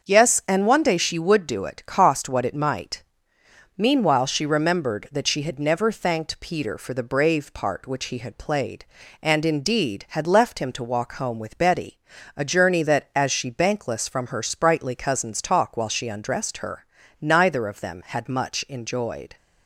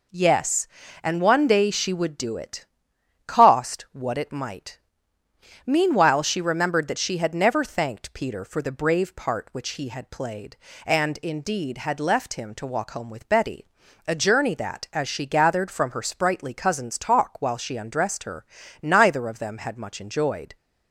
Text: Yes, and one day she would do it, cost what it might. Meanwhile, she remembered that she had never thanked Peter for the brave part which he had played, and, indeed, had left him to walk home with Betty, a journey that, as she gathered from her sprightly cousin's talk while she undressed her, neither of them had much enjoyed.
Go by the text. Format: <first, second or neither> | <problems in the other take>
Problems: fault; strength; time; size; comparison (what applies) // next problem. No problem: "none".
second | starts louder than the rest; until 1.1 s; 6.5 dB // says "bankless" for "gathered"; at 13.4 s